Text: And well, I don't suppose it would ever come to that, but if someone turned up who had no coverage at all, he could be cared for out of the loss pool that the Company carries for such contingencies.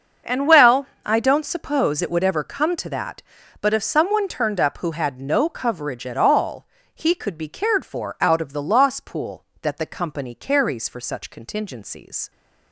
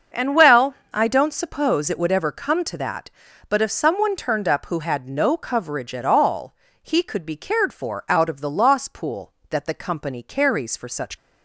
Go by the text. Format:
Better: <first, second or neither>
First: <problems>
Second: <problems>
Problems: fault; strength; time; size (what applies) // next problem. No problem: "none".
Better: first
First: starts louder than the rest; until 1.4 s; 6.5 dB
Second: starts louder than the rest; until 1.3 s; 6.5 dB // stops before "contingencies"; at 11.1 s